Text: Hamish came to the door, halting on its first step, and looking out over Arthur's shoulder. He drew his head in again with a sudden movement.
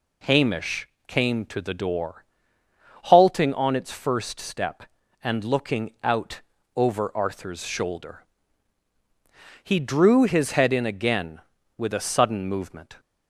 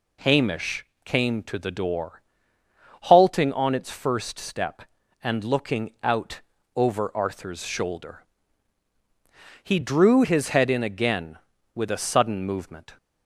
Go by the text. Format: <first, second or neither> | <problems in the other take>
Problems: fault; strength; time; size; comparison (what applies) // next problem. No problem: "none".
neither | pauses between "Hamish" and "came"; slight; the same in both // pauses between "out" and "over"; slight; the same in both